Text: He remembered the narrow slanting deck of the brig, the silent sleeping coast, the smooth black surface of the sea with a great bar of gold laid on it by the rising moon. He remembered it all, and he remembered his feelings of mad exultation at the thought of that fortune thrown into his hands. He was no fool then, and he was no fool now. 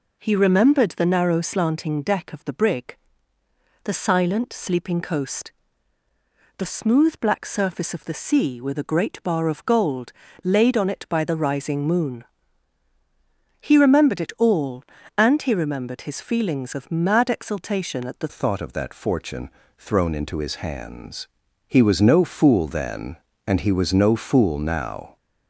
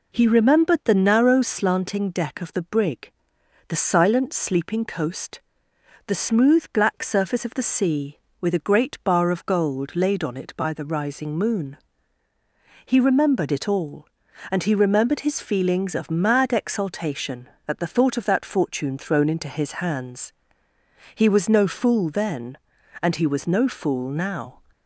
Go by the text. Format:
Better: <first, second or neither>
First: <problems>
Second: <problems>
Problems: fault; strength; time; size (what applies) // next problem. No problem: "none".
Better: second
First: pauses between "gold" and "laid"; slight; at 10.1 s; 0.32 s long // changes voice at "thought"; from 18.2 s on; 6.9 s long // pauses between "fortune" and "thrown"; slight; at 19.4 s; 0.28 s long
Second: none